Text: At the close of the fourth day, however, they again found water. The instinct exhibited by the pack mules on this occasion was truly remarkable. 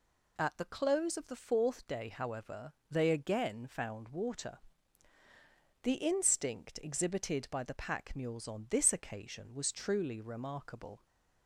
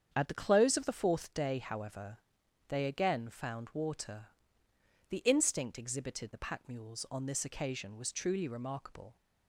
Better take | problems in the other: first | starts louder than the rest; strong; until 1.1 s; 8 dB // skips "by"; at 6.3 s

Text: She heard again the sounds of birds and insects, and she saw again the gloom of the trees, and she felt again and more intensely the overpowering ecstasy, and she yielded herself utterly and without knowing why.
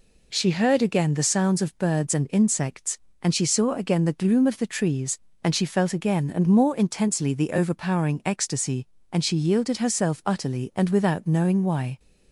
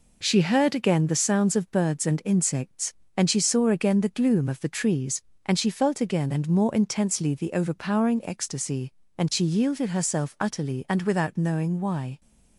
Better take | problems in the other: first | gets quieter; noticeable; throughout; 5.5 dB

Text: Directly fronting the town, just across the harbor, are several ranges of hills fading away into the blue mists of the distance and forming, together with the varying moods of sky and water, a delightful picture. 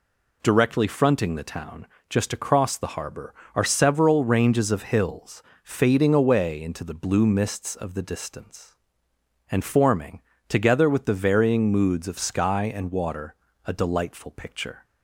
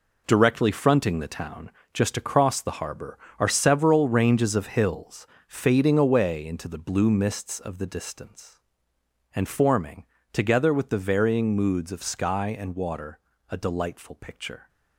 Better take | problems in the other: first | gets quieter; strong; throughout; 9 dB // pauses between "hills" and "fading"; slight; at 5.2 s; 0.20 s long; slight in the first

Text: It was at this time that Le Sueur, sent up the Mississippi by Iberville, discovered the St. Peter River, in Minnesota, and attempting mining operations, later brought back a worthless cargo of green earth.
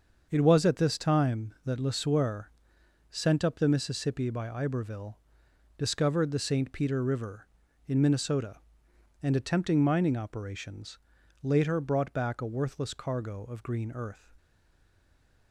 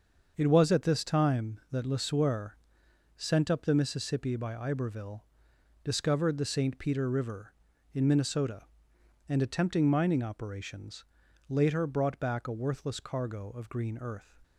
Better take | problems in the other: second | starts louder than the rest; until 1.3 s; 6.5 dB; also in the second // stays silent after the last word; from 14.3 s on; 1.2 s long

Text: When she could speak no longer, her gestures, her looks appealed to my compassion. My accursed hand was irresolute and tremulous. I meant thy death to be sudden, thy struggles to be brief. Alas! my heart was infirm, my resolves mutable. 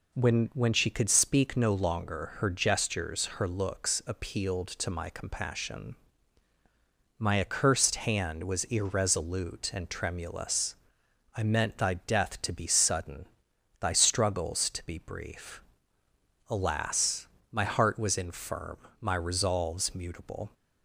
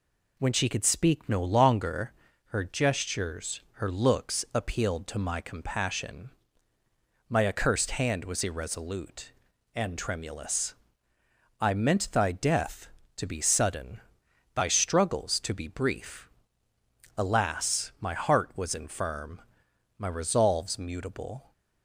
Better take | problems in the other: second | says "When" twice; at 0.5 s

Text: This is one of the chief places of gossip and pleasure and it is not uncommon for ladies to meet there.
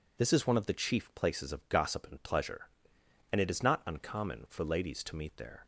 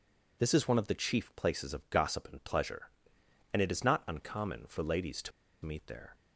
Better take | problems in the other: first | pauses between "to" and "meet"; slight; at 5.3 s; 0.32 s long

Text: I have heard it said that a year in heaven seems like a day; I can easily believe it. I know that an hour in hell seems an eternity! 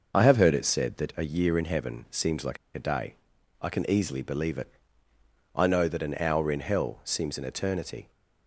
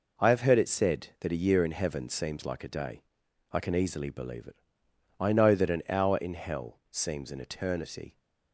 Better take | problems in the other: second | pauses between "like" and "a"; slight; at 2.5 s; 0.18 s long

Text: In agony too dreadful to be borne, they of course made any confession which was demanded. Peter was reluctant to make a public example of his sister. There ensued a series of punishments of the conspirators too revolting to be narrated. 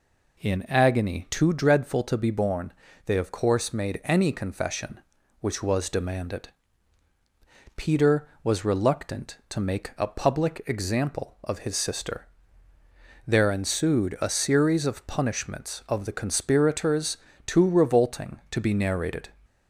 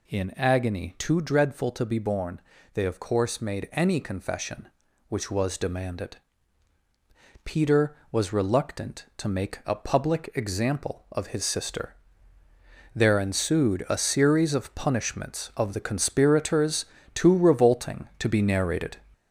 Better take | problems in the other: first | gets louder; noticeable; throughout; 4.5 dB // pauses between "conspirators" and "too"; slight; at 16.8 s; 0.28 s long; slight in the first

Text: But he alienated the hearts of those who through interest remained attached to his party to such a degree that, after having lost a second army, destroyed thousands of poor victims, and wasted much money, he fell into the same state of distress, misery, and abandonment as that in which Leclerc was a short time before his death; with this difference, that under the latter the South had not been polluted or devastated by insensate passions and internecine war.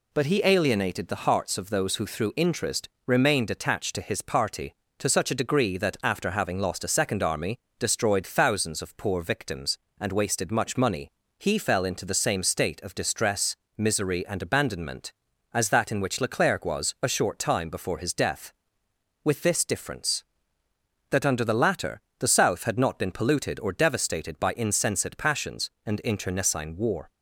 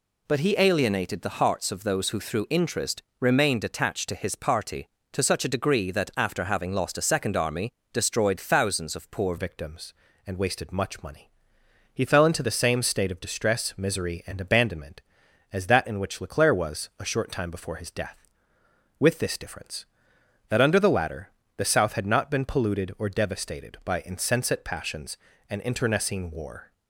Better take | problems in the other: first | pauses between "interest" and "remained"; slight; at 3.0 s; 0.18 s long; slight in the first // changes voice at "victims"; from 9.3 s on; 17.4 s long // pauses between "latter" and "the"; slight; at 21.3 s; 0.26 s long; slight in the first

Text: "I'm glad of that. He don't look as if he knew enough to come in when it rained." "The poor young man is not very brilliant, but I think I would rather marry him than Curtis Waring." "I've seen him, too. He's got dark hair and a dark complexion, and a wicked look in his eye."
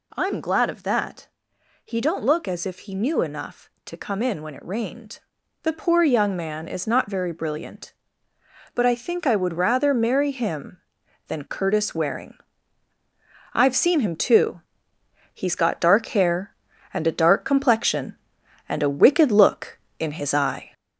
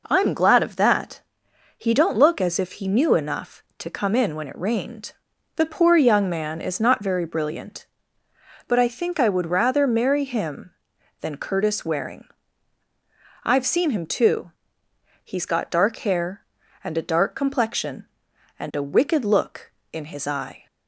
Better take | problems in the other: second | gets louder; noticeable; throughout; 4 dB

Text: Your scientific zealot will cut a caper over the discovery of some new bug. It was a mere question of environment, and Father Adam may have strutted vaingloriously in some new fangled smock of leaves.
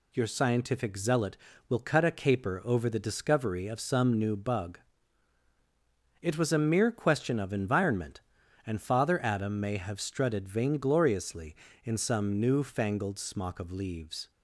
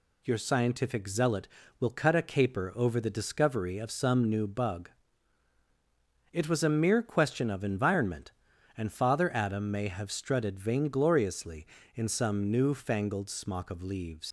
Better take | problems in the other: first | leaves "leaves" unfinished; at 14.2 s; 100 ms

